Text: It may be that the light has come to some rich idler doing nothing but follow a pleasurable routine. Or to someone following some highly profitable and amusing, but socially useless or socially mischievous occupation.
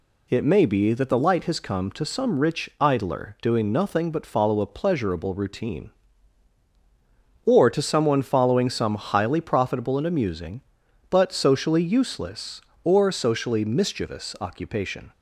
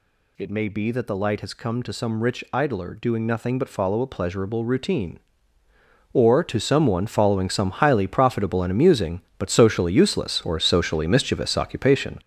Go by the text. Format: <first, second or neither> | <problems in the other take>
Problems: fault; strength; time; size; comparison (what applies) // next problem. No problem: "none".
first | gets louder; strong; throughout; 7.5 dB